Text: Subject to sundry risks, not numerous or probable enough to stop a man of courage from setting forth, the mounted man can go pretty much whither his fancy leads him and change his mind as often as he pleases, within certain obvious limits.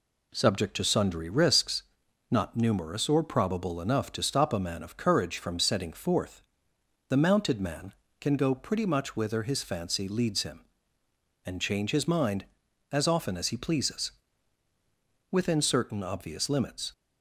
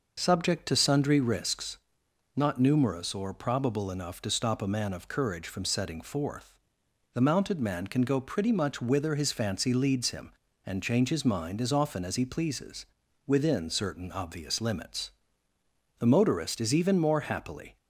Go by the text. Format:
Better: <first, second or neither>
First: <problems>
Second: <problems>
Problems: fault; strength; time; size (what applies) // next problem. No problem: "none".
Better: first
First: none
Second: goes on to say "The motorist is even more happily"; strong; from 16.0 s on; 1.7 s long